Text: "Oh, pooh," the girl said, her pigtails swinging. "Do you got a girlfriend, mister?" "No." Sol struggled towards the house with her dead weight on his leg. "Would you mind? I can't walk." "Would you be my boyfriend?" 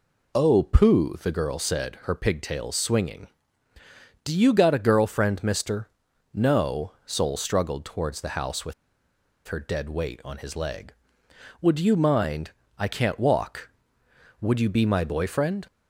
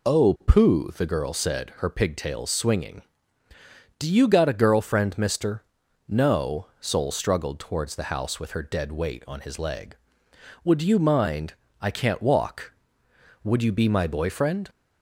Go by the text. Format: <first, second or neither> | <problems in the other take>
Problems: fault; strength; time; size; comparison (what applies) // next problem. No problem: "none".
second | pauses between "with" and "her"; noticeable; at 8.7 s; 0.74 s long